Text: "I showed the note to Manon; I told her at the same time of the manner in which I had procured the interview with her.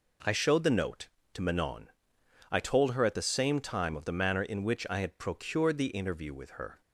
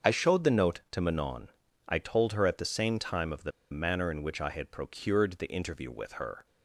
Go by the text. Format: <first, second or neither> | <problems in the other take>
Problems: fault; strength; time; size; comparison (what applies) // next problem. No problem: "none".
first | starts louder than the rest; until 1.1 s; 7 dB // pauses between "the" and "manner"; slight; at 3.5 s; 0.20 s long